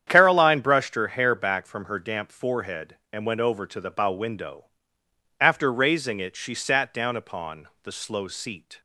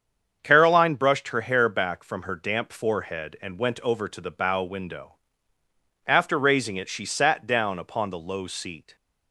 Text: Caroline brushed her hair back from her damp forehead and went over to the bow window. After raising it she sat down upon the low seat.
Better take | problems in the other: second | starts louder than the rest; strong; until 1.0 s; 9 dB; strong in the second // says "slow" for "low"; at 7.9 s

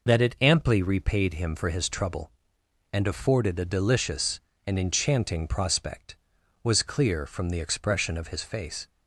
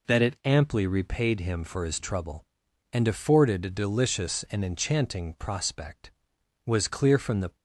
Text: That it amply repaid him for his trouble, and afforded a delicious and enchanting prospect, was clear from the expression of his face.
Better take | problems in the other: first | stops before "expression of his face"; at 7.5 s

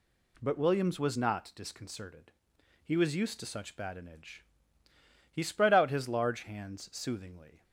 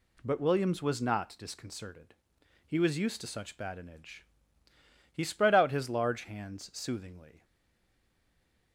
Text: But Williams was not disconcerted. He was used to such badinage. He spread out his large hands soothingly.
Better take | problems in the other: first | stays silent after the last word; noticeable; from 7.4 s on; 1.3 s long

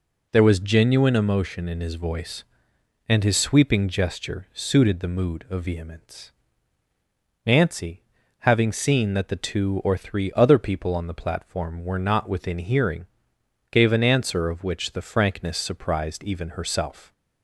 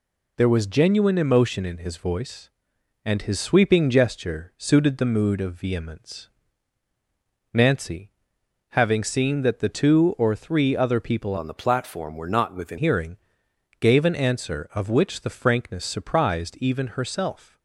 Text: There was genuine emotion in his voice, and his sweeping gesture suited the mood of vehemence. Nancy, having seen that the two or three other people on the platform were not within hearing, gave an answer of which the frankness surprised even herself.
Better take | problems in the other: first | changes voice from "on" to "within"; from 11.3 to 12.7 s; 1.4 s long

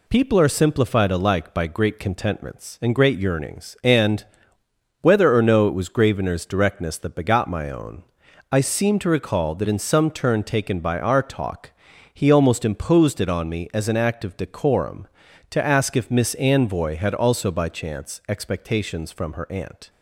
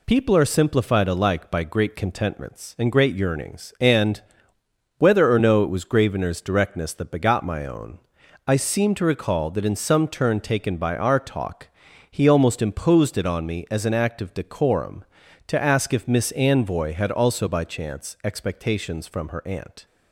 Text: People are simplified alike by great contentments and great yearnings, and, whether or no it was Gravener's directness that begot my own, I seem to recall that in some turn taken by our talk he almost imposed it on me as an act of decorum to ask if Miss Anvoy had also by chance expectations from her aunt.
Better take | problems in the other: neither | pauses between "talk" and "he"; the same in both

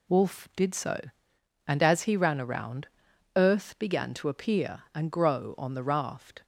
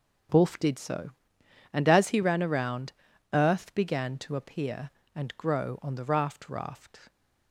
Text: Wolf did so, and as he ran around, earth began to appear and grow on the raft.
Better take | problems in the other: first | starts louder than the rest; strong; until 1.9 s; 7.5 dB // says "raft" twice; at 6.4 s

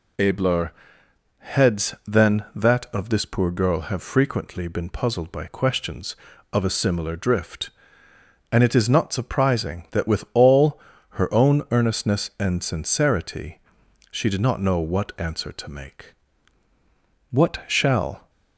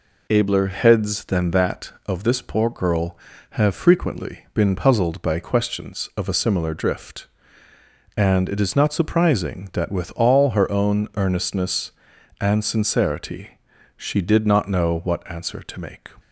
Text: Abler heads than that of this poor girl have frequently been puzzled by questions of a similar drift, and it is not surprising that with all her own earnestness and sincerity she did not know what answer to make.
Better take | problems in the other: second | pauses between "Abler" and "heads"; noticeable; at 0.7 s; 0.66 s long // pauses between "all" and "her"; slight; at 10.7 s; 0.30 s long // pauses between "sincerity" and "she"; noticeable; at 13.5 s; 0.50 s long; also in the second // goes on to say "What shall"; noticeable; from 17.3 s on; 0.98 s long

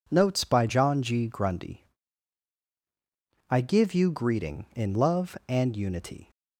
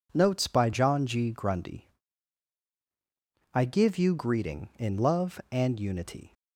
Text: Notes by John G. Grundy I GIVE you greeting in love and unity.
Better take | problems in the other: neither | pauses between "Grundy" and "I"; strong; the same in both

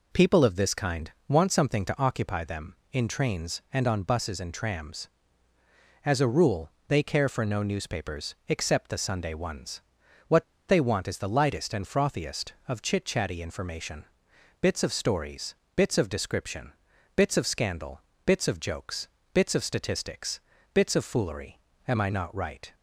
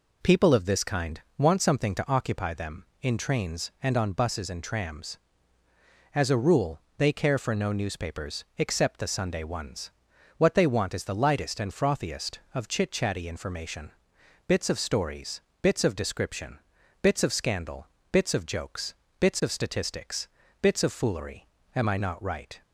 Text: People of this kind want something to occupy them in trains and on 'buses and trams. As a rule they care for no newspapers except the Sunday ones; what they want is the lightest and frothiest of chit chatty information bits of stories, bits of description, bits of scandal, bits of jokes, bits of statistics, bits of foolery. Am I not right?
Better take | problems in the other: second | pauses between "kind" and "want"; slight; at 1.1 s; 0.16 s long; slight in the second // pauses between "rule" and "they"; slight; at 6.7 s; 0.18 s long; slight in the second // pauses between "what" and "they"; slight; at 10.4 s; 0.23 s long // pauses between "information" and "bits"; noticeable; at 14.0 s; 0.56 s long; noticeable in the second

